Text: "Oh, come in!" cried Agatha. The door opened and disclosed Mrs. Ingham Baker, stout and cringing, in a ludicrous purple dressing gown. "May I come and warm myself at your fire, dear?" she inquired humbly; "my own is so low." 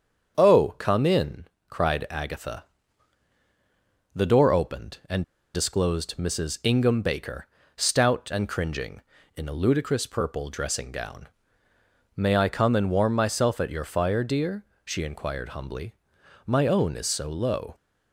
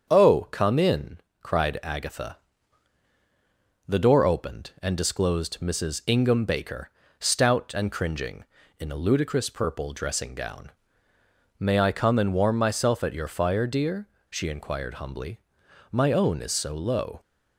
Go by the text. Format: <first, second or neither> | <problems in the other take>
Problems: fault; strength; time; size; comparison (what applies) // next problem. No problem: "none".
second | starts louder than the rest; strong; until 1.4 s; 7 dB; strong in the second // pauses between "and" and "disclosed"; slight; at 5.2 s; 0.31 s long